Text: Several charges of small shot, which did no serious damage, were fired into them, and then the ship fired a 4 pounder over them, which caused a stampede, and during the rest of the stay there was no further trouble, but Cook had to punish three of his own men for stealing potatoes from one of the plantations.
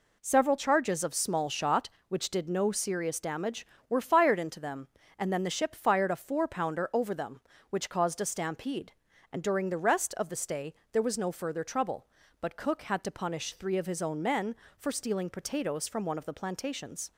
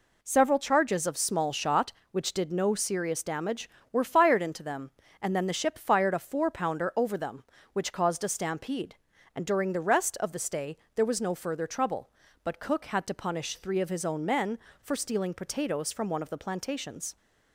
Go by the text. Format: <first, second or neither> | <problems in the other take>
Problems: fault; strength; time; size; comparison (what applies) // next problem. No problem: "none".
neither | pauses between "stay" and "there"; slight; the same in both